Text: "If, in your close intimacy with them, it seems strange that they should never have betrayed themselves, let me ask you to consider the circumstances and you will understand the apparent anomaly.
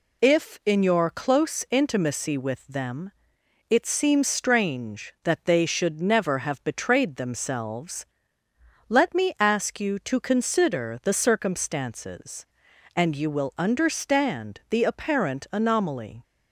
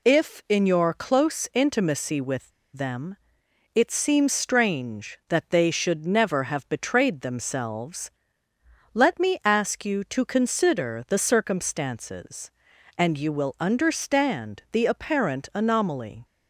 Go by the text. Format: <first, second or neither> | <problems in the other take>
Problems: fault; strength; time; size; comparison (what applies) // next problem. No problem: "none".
first | pauses between "with" and "them"; slight; at 2.4 s; 0.24 s long